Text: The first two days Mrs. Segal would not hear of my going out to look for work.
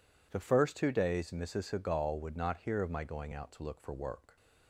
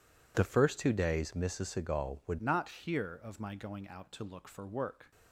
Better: first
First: none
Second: changes voice at "not"; from 2.4 s on; 2.7 s long

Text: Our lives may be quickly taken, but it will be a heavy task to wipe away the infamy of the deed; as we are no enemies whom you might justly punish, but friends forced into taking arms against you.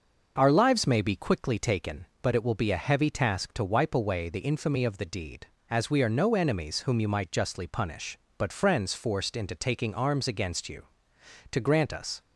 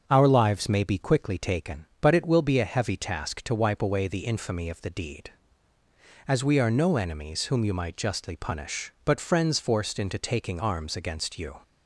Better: second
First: starts louder than the rest; noticeable; until 1.3 s; 6 dB // goes on to say "To grant us"; noticeable; from 11.5 s on; 0.68 s long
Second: starts louder than the rest; until 1.0 s; 7 dB

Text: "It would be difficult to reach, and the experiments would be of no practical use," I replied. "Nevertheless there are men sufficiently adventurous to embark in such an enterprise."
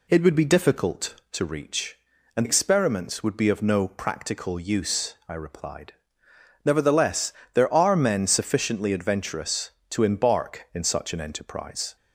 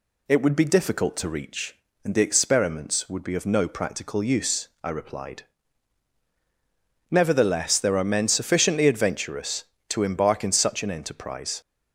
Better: second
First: skips "the"; at 2.4 s // pauses between "Nevertheless" and "there"; slight; at 7.3 s; 0.22 s long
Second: none

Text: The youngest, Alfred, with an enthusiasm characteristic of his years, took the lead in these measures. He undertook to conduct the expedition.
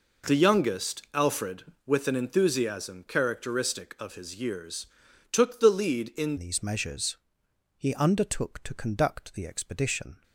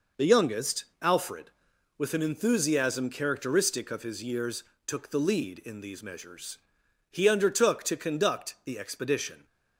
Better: second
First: changes voice at "these"; from 6.3 s on; 3.9 s long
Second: none

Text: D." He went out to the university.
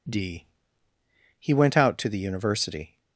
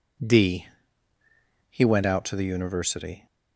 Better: neither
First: none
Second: none

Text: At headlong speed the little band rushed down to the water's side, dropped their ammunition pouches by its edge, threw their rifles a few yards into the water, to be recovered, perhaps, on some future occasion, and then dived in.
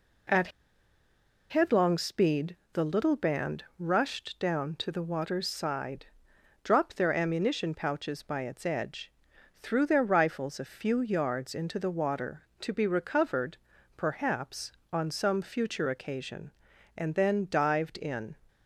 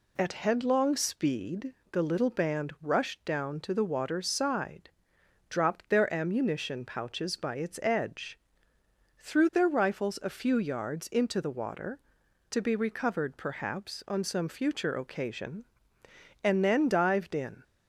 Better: second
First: pauses between "At" and "headlong"; at 0.4 s; 1.0 s long // pauses between "speed" and "the"; slight; at 2.5 s; 0.16 s long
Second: pauses between "speed" and "the"; slight; at 1.7 s; 0.18 s long

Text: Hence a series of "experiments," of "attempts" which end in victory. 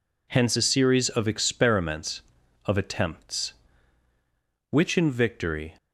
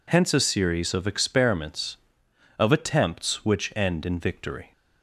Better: second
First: skips "end"; at 4.9 s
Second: none

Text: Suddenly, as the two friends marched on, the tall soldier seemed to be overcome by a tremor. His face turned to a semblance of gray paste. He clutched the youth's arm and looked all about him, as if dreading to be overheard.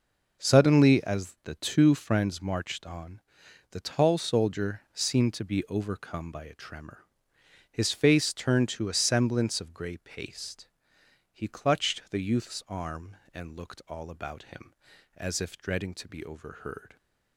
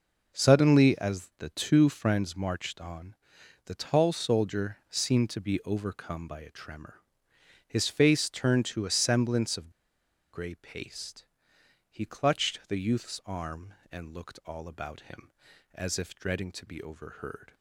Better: first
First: none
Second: pauses between "of" and "gray"; noticeable; at 9.7 s; 0.62 s long

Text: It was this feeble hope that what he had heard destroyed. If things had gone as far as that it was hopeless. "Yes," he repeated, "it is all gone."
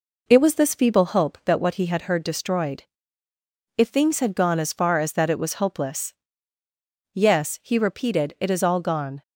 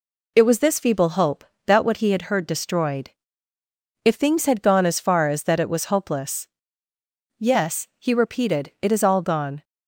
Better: second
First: starts louder than the rest; noticeable; until 1.4 s; 4.5 dB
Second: none

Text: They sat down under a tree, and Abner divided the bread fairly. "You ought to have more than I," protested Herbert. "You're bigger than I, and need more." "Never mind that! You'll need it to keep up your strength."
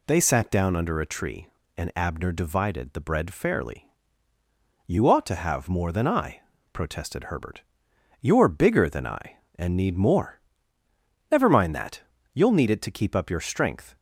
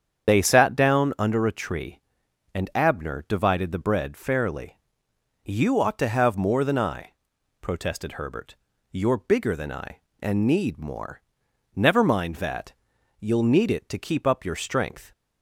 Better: first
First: none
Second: loses the start of "They"; at 0.2 s; 40 ms // starts louder than the rest; strong; until 1.3 s; 8 dB

